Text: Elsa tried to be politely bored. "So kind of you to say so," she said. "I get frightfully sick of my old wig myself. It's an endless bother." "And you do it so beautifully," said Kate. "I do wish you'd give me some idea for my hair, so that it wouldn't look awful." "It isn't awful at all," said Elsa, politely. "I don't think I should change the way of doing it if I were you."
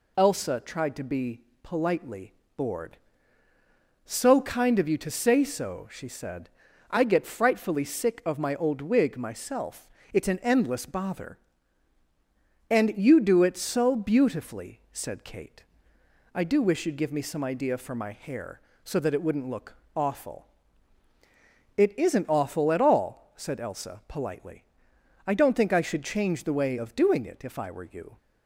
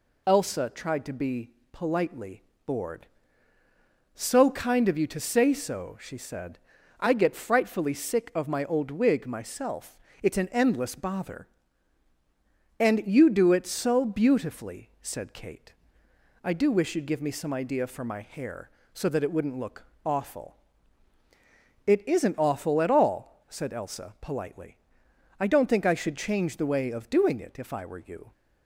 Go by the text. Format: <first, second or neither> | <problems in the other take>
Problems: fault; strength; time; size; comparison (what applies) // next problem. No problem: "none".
neither | pauses between "be" and "politely"; slight; the same in both // pauses between "politely" and "bored"; slight; the same in both // pauses between "look" and "awful"; slight; the same in both